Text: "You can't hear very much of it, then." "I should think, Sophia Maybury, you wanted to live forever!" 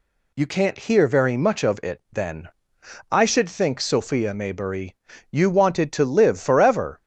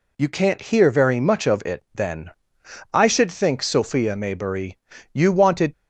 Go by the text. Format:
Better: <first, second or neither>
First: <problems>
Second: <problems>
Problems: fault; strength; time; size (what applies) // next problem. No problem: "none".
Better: first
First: none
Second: stops before "to live forever"; at 5.7 s